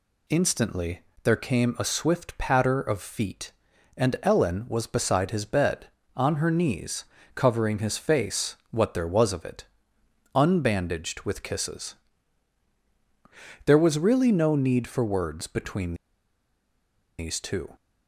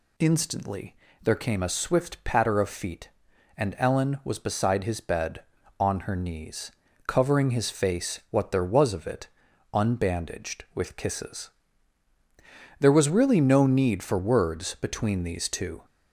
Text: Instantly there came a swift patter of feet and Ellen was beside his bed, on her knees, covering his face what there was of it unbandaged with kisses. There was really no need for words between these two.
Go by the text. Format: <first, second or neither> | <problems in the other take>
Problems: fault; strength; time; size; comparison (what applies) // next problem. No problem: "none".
second | pauses between "Instantly" and "there"; slight; at 1.0 s; 0.22 s long; slight in the second // pauses between "it" and "unbandaged"; noticeable; at 9.6 s; 0.70 s long; noticeable in the second // pauses between "between" and "these"; at 15.9 s; 1.2 s long